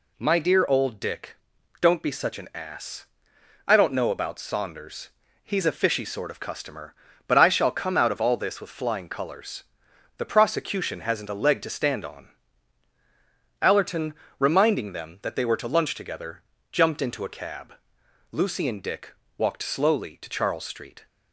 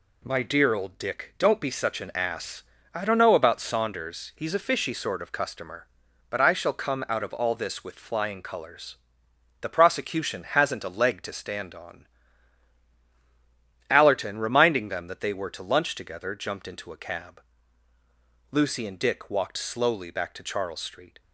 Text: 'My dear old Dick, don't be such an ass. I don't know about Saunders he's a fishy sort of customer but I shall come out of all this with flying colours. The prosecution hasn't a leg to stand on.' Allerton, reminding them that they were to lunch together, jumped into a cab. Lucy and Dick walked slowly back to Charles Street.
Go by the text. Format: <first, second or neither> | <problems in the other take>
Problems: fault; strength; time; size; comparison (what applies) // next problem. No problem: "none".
second | pauses between "Saunders" and "he's"; slight; at 5.1 s; 0.36 s long // pauses between "Dick" and "walked"; slight; at 19.1 s; 0.24 s long // skips "back"; at 20.1 s